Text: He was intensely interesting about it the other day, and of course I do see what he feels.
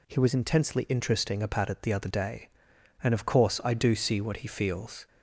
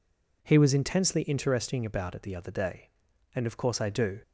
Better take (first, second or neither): first